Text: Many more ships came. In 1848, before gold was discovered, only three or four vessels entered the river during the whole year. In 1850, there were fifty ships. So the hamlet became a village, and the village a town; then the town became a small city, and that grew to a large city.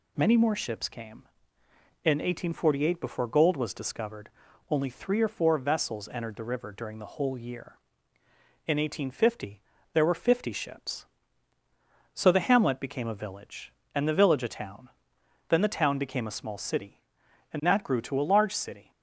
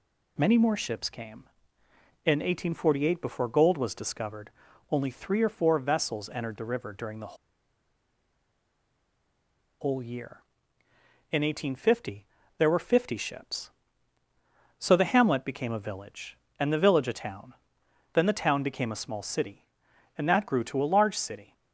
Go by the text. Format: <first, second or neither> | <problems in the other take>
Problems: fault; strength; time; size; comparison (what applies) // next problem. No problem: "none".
first | pauses between "the" and "whole"; strong; at 7.3 s; 2.4 s long